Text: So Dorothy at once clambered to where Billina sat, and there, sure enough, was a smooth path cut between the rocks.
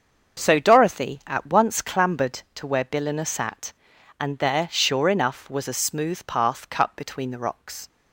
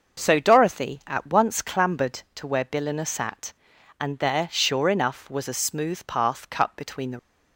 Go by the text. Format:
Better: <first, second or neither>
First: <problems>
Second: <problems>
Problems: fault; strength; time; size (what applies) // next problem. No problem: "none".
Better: first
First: starts louder than the rest; until 1.4 s; 6.5 dB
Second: starts louder than the rest; noticeable; until 1.2 s; 6 dB // stops before "rocks"; at 7.1 s